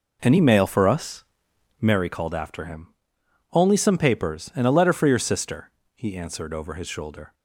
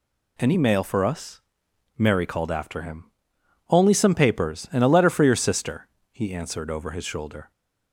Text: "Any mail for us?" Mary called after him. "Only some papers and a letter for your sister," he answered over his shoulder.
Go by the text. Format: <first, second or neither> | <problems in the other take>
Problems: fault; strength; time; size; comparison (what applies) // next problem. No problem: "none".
second | starts louder than the rest; noticeable; until 2.0 s; 4.5 dB